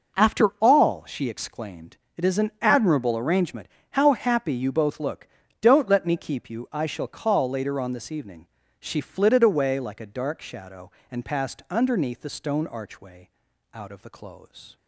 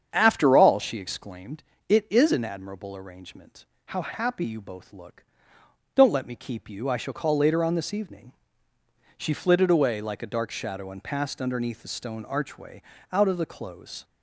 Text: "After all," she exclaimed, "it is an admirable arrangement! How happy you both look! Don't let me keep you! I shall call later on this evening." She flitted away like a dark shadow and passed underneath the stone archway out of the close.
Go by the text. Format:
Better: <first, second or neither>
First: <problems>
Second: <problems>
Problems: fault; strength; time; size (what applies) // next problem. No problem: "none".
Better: first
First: pauses between "archway" and "out"; at 13.2 s; 0.42 s long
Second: starts louder than the rest; strong; until 1.4 s; 7.5 dB // pauses between "archway" and "out"; slight; at 12.8 s; 0.32 s long